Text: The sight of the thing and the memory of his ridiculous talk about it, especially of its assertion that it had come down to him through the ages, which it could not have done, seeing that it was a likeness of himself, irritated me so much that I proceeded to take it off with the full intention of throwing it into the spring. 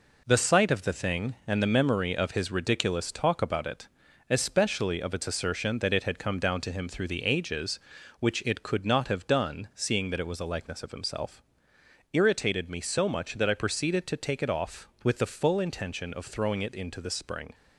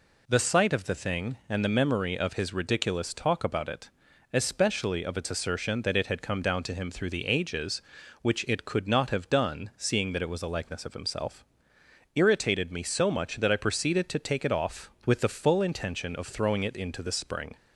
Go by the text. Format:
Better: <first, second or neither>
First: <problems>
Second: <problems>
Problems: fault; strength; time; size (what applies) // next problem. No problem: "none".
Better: second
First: gets quieter; noticeable; throughout; 5.5 dB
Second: none